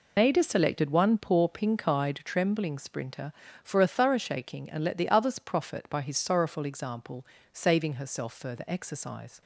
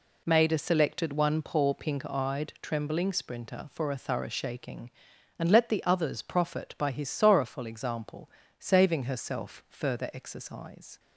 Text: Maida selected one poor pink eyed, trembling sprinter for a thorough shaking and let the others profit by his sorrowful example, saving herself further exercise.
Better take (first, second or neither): second